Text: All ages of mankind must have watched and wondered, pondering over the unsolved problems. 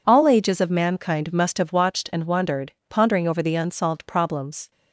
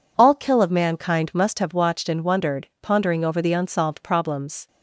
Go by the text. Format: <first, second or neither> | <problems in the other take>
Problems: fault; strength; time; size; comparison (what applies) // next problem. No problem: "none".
first | says "kill" for "ages"; at 0.3 s